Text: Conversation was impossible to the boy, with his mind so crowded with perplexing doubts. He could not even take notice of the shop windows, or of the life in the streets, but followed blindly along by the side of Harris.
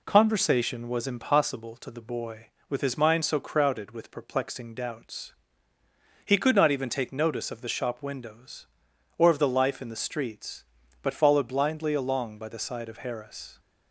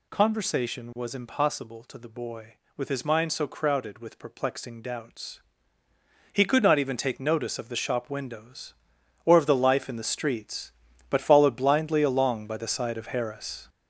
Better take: first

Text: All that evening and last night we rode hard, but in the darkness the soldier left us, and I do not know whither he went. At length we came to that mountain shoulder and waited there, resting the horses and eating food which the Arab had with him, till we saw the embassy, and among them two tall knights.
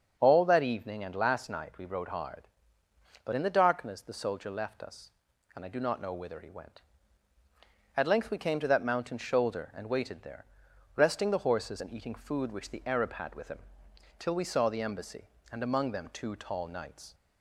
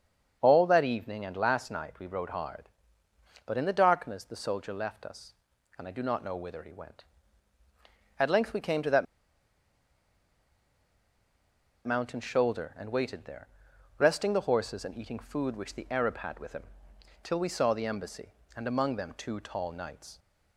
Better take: first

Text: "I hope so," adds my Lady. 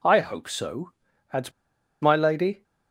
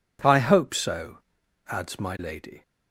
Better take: second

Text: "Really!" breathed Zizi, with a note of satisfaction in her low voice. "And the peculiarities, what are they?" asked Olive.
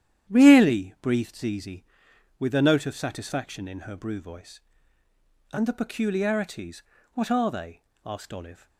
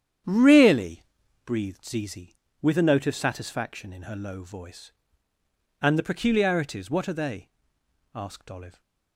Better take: second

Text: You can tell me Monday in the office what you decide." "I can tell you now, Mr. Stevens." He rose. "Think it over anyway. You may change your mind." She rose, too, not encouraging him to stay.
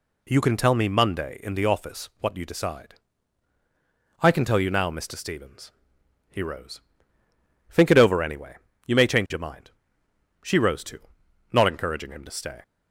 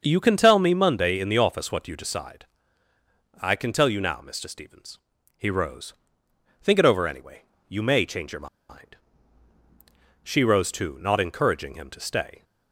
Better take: first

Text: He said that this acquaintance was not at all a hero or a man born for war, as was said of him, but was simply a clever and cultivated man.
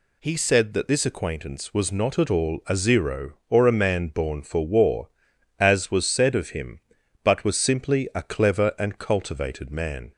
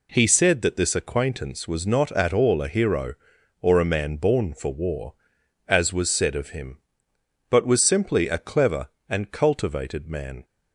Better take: second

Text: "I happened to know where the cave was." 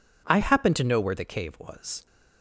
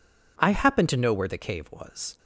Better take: neither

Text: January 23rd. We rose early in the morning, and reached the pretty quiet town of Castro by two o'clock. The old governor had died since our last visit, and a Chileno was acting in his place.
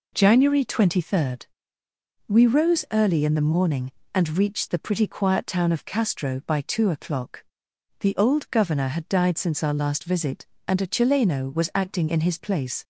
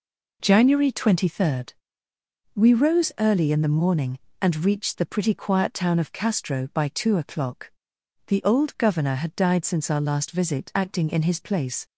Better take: first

